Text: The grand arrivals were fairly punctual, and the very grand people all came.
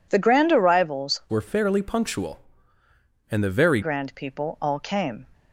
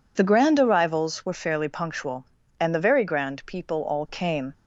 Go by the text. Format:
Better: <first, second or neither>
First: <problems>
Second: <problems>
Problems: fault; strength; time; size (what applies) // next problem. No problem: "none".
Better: second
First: changes voice from "were" to "very"; from 1.2 to 3.8 s; 2.6 s long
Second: none